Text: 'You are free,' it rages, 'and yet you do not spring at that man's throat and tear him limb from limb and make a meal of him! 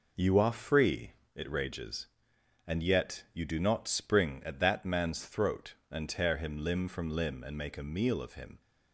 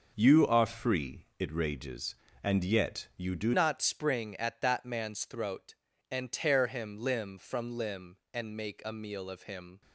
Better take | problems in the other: first | changes voice at "not"; from 3.5 s on; 6.3 s long

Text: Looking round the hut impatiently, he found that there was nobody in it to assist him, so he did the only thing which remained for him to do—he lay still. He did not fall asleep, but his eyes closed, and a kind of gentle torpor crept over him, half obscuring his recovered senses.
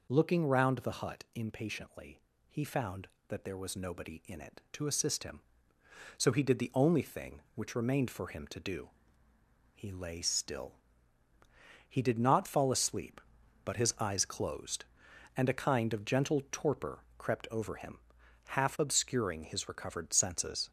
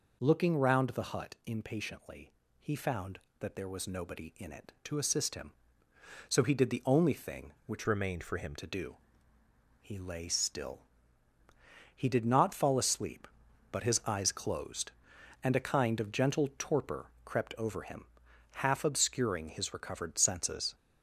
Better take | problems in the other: first | changes voice from "remained" to "him"; from 7.8 to 8.5 s; 0.7 s long

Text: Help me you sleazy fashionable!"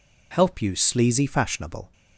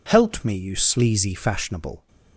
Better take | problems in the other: second | skips "me"; at 0.6 s

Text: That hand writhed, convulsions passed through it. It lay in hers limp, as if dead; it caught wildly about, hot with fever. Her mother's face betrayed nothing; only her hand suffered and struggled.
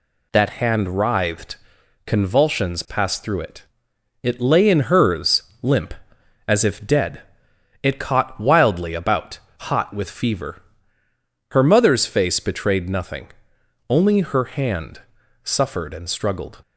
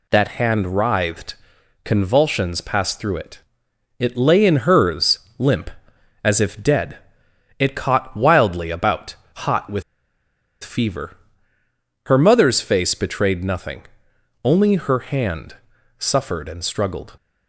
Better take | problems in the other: first | pauses between "hers" and "limp"; slight; at 5.1 s; 0.18 s long; slight in the first // pauses between "with" and "fever"; noticeable; at 9.8 s; 0.81 s long // pauses between "hand" and "suffered"; at 15.5 s; 0.42 s long; also in the first

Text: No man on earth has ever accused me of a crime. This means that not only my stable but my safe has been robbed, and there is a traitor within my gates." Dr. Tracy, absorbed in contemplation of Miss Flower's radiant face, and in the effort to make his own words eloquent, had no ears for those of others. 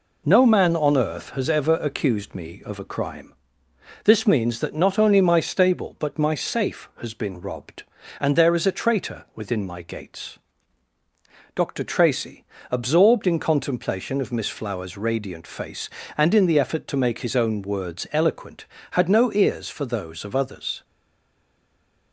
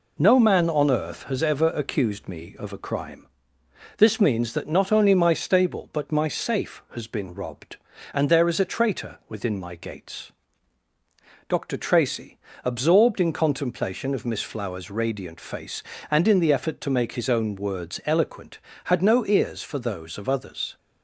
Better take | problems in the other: second | stays silent after the last word; noticeable; from 20.8 s on; 1.3 s long

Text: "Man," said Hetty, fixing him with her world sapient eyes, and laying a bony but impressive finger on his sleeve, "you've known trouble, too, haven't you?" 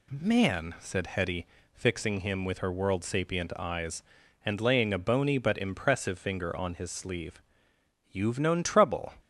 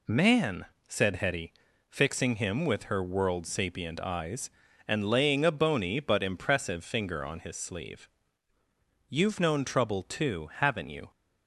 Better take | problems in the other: second | stops before "too haven't you"; at 9.2 s

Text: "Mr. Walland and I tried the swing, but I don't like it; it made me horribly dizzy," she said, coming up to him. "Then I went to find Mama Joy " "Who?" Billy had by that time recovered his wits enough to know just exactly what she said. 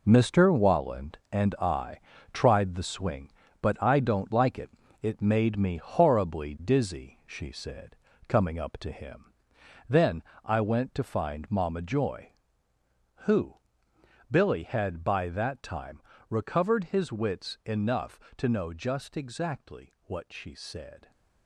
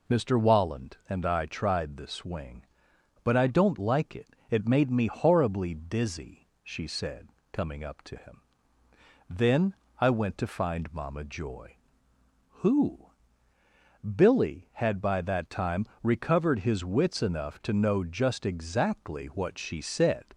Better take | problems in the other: second | gets quieter; strong; throughout; 10 dB // pauses between "I" and "tried"; slight; at 1.9 s; 0.34 s long // pauses between "Then" and "I"; slight; at 10.2 s; 0.22 s long; slight in the second // pauses between "time" and "recovered"; slight; at 16.0 s; 0.28 s long; slight in the second

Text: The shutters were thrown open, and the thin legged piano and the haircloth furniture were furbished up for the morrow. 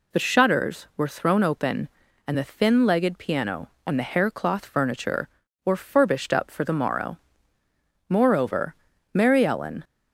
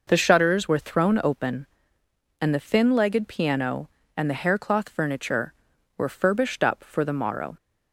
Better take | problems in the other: second | goes on to say "Moreover Mary Ellen"; strong; from 8.0 s on; 1.7 s long

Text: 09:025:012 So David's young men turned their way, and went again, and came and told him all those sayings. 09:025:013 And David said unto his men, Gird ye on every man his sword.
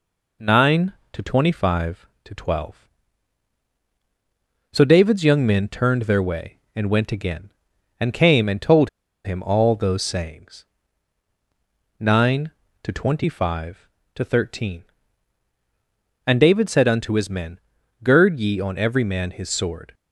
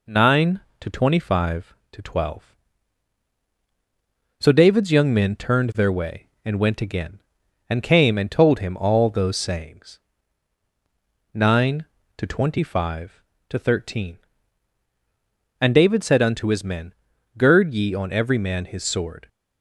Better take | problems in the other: second | pauses between "told" and "him"; at 8.8 s; 0.36 s long

